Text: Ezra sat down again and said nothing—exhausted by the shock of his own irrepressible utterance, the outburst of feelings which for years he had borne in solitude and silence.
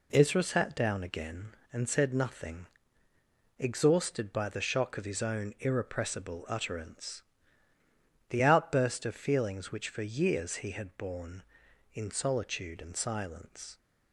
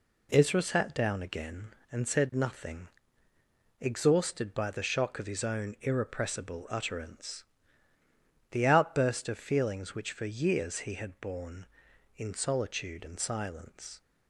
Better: neither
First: none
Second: none

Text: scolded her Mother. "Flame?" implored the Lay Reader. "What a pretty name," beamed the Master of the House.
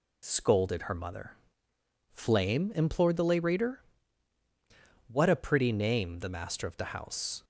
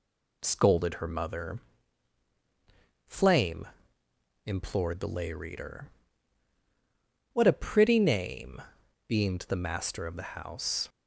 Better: second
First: skips "beamed"; at 6.1 s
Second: none

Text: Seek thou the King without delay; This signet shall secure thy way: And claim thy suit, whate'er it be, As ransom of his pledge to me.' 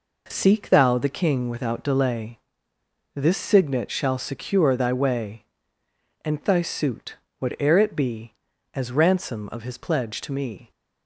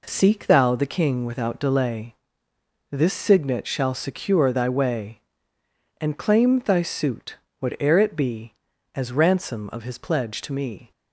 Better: second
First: skips "claim"; at 6.4 s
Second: none

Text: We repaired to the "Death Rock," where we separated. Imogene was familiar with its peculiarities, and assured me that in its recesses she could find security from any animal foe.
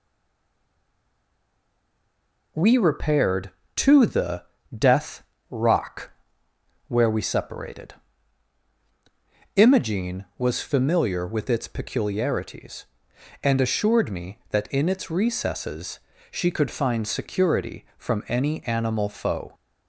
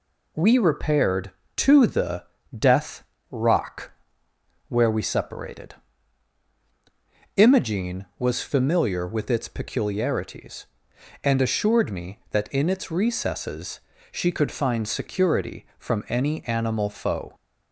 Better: second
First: stays silent before the first word; strong; until 2.5 s; 2.5 s long // pauses between "the" and "Death"; slight; at 4.4 s; 0.32 s long // pauses between "Death" and "Rock"; slight; at 5.2 s; 0.26 s long // pauses between "recesses" and "she"; slight; at 15.9 s; 0.32 s long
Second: pauses between "the" and "Death"; slight; at 2.2 s; 0.32 s long // pauses between "Death" and "Rock"; slight; at 3.0 s; 0.26 s long // pauses between "recesses" and "she"; slight; at 13.7 s; 0.32 s long

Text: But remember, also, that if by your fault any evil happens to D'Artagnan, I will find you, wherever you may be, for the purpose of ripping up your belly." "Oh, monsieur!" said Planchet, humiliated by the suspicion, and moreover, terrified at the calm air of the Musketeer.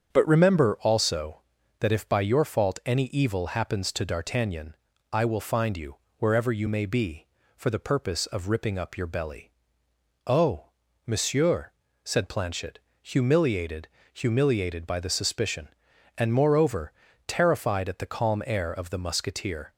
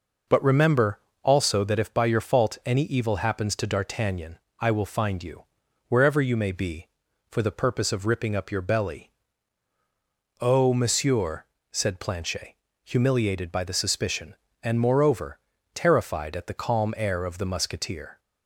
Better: second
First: starts louder than the rest; strong; until 1.1 s; 8 dB // says "humiliated" twice; at 14.1 s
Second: none

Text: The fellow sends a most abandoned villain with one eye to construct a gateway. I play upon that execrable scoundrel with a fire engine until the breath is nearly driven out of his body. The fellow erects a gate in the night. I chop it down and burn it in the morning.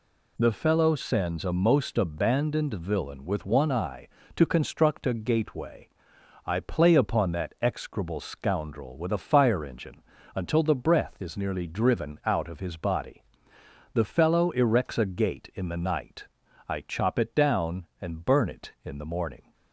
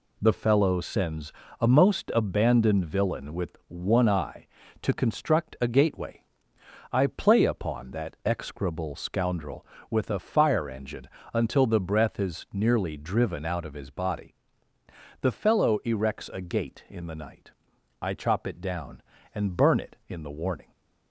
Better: first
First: pauses between "engine" and "until"; slight; at 10.0 s; 0.32 s long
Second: pauses between "sends" and "a"; slight; at 1.3 s; 0.30 s long // pauses between "engine" and "until"; slight; at 11.0 s; 0.26 s long // says "warning" for "morning"; at 20.3 s

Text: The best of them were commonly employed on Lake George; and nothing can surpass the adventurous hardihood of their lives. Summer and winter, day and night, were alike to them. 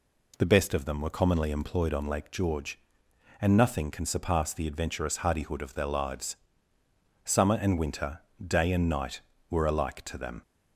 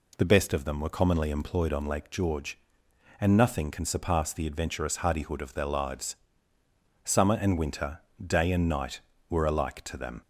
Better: neither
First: none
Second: none

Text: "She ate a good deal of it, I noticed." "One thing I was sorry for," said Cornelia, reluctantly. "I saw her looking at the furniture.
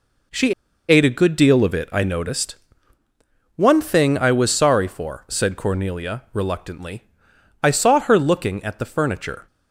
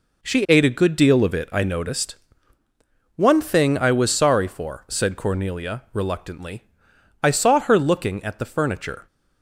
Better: second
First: pauses between "She" and "ate"; slight; at 0.5 s; 0.35 s long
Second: none

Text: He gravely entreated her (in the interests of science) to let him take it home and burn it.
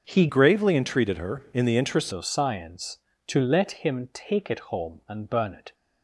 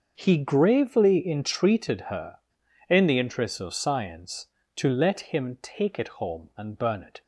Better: second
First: starts louder than the rest; until 1.0 s; 6.5 dB // changes voice from "gravely" to "interests"; from 0.2 to 2.1 s; 1.9 s long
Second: starts louder than the rest; until 1.1 s; 6.5 dB

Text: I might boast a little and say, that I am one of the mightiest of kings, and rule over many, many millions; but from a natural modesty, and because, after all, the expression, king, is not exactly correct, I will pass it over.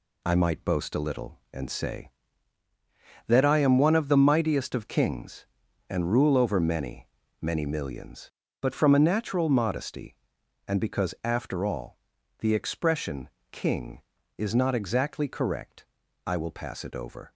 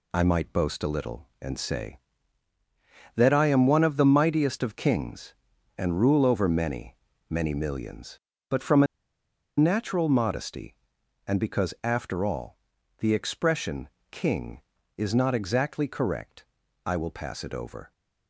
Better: first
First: none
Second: pauses between "a" and "natural"; noticeable; at 8.8 s; 0.73 s long

